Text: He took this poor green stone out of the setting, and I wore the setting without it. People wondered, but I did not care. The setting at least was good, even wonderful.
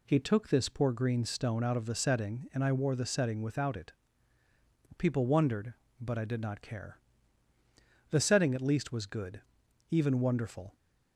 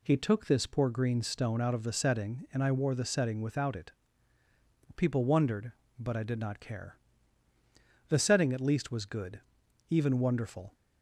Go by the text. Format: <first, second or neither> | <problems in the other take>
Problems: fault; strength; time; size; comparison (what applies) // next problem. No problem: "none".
neither | none